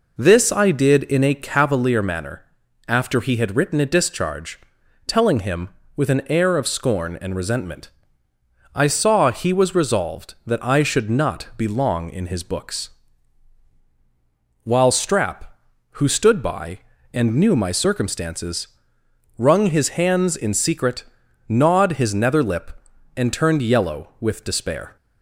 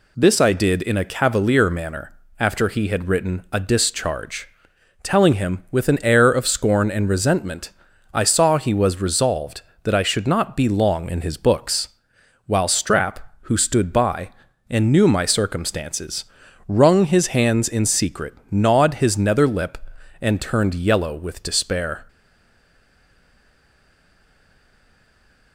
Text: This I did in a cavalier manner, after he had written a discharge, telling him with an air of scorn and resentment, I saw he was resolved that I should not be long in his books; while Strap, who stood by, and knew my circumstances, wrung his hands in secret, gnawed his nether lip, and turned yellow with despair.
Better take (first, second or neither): first